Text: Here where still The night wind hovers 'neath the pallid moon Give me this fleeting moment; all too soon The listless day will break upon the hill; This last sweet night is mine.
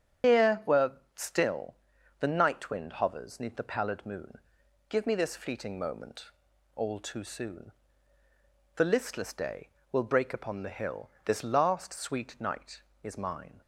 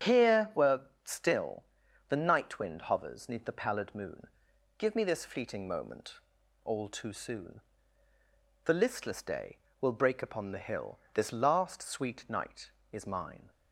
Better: second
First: loses the start of "Here"; at 0.2 s; 120 ms // starts louder than the rest; strong; until 1.5 s; 9 dB // pauses between "where" and "still"; slight; at 0.9 s; 0.24 s long // pauses between "still" and "The"; noticeable; at 1.7 s; 0.46 s long // pauses between "moon" and "Give"; noticeable; at 4.3 s; 0.52 s long // pauses between "soon" and "The"; at 7.7 s; 1.0 s long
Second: starts louder than the rest; strong; until 1.3 s; 9 dB // pauses between "where" and "still"; slight; at 0.7 s; 0.24 s long // pauses between "still" and "The"; noticeable; at 1.6 s; 0.46 s long // pauses between "moon" and "Give"; noticeable; at 4.2 s; 0.52 s long // pauses between "soon" and "The"; at 7.5 s; 1.0 s long

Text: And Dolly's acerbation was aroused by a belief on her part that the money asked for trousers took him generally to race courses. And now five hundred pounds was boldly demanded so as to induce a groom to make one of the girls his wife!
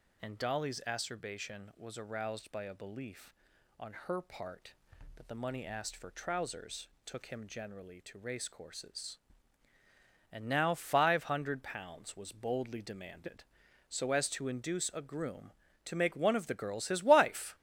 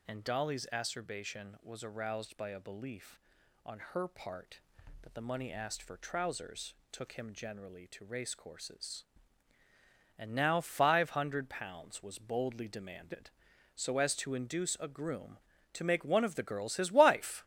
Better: neither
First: pauses between "trousers" and "took"; slight; at 6.8 s; 0.18 s long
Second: pauses between "trousers" and "took"; slight; at 6.7 s; 0.18 s long

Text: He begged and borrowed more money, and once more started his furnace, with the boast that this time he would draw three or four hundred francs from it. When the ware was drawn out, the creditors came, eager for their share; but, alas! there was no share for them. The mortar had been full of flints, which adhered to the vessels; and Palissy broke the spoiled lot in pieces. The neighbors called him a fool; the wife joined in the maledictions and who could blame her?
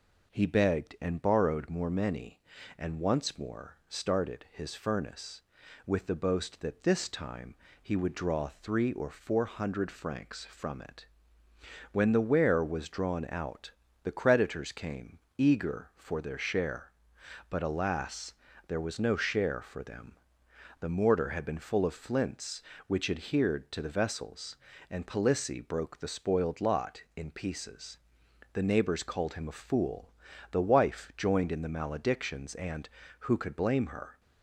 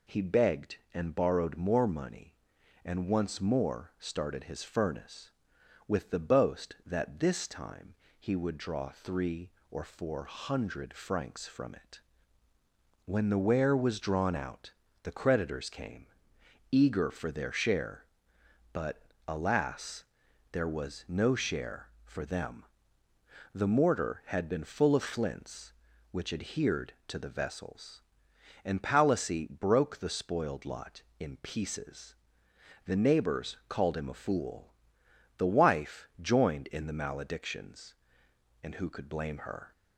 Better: second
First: says "many" for "money"; at 1.8 s // pauses between "time" and "he"; slight; at 7.5 s; 0.26 s long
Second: pauses between "time" and "he"; slight; at 7.9 s; 0.24 s long

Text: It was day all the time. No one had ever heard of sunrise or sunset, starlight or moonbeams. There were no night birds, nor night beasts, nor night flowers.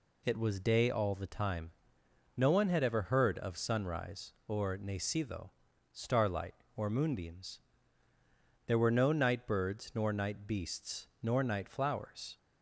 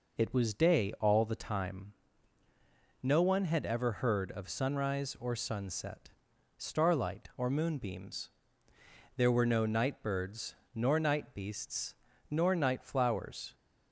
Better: second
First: says "nacido" for "sunset"; at 4.7 s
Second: none

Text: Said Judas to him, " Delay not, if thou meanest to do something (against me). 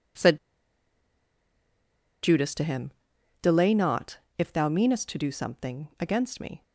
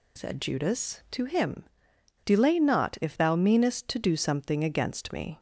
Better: second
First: pauses between "Said" and "Judas"; strong; at 0.3 s; 1.8 s long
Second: none

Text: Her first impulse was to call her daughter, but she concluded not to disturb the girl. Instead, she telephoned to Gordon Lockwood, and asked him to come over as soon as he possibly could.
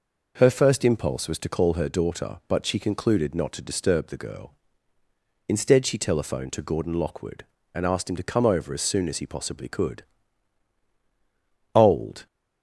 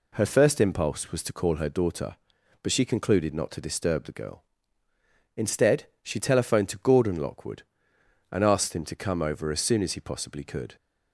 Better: second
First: goes on to say "Old"; from 11.7 s on; 0.52 s long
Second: none

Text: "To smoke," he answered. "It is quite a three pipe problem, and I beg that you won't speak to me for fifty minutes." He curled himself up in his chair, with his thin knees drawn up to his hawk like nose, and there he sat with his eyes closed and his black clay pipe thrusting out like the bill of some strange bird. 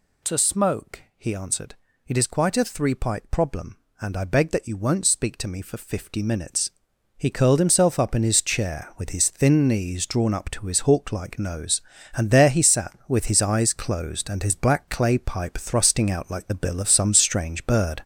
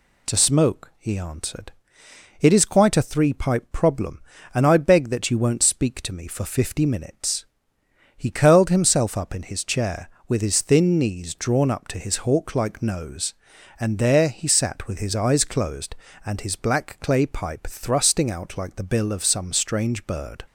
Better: second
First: gets louder; noticeable; throughout; 5 dB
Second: none

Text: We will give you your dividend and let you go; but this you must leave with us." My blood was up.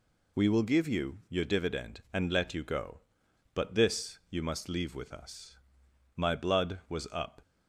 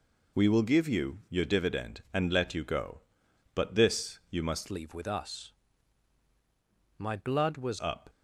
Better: first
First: none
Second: changes voice from "leave" to "was"; from 4.7 to 7.7 s; 3.0 s long

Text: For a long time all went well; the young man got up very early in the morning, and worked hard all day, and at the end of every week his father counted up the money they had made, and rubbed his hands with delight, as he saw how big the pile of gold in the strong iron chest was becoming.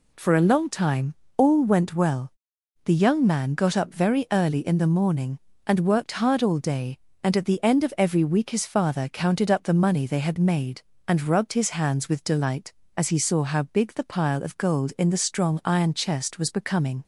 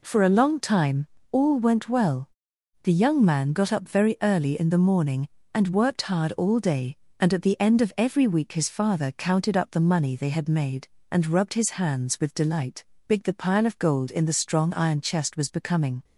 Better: first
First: pauses between "time" and "all"; slight; at 1.1 s; 0.20 s long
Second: pauses between "time" and "all"; slight; at 1.0 s; 0.24 s long // skips "as he saw how"; at 12.9 s

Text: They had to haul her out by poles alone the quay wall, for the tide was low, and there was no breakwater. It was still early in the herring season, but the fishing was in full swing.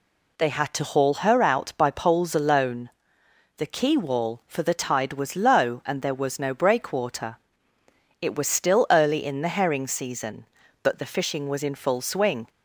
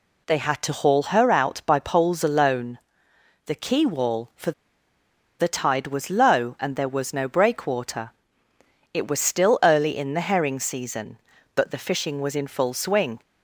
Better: first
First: pauses between "alone" and "the"; noticeable; at 2.8 s; 0.68 s long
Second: pauses between "alone" and "the"; noticeable; at 2.7 s; 0.68 s long // pauses between "for" and "the"; noticeable; at 4.5 s; 0.87 s long

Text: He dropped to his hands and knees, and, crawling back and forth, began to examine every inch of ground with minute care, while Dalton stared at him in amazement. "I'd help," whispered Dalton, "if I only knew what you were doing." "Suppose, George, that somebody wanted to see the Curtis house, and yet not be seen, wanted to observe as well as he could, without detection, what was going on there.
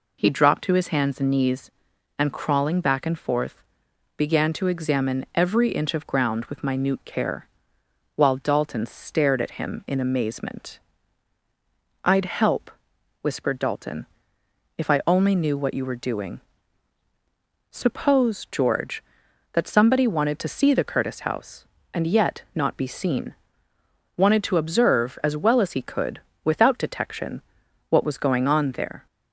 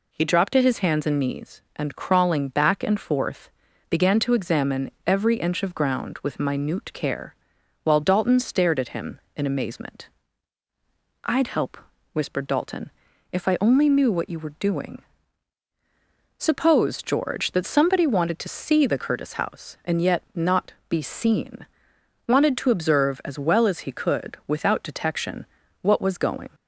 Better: first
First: none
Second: pauses between "examine" and "every"; slight; at 4.9 s; 0.16 s long // stops before "on there"; at 26.5 s

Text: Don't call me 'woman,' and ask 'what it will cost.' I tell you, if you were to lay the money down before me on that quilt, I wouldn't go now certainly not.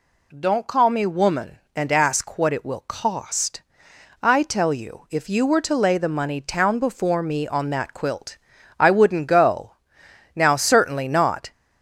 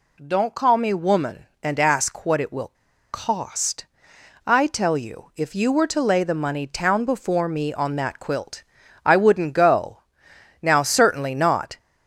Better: first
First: pauses between "go" and "now"; noticeable; at 9.7 s; 0.62 s long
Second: pauses between "will" and "cost"; at 2.7 s; 0.41 s long // pauses between "go" and "now"; noticeable; at 9.9 s; 0.62 s long

